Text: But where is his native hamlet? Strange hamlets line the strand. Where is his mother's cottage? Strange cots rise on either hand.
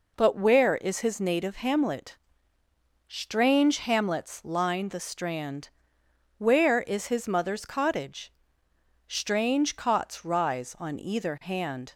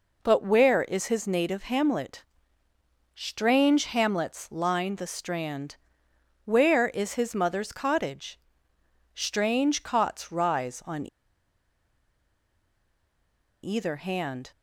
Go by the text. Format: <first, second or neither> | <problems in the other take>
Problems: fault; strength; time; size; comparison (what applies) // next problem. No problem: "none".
first | pauses between "on" and "either"; strong; at 11.0 s; 2.5 s long